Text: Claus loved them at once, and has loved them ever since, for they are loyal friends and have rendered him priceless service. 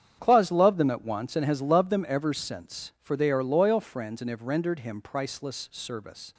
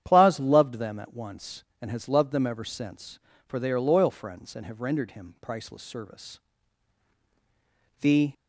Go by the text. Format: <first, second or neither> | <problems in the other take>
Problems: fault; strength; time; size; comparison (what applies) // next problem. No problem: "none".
first | starts louder than the rest; strong; until 1.0 s; 9.5 dB; strong in the first // goes on to say "The"; slight; from 8.0 s on; 0.32 s long